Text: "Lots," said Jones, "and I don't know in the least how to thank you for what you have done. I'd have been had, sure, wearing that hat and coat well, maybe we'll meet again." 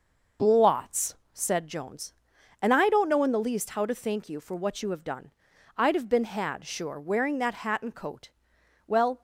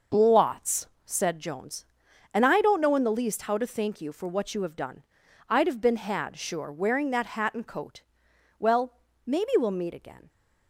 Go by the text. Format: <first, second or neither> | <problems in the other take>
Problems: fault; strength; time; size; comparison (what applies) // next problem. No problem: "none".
second | pauses between "coat" and "well"; noticeable; at 8.3 s; 0.56 s long; noticeable in the second // stops before "maybe we'll meet again"; at 9.1 s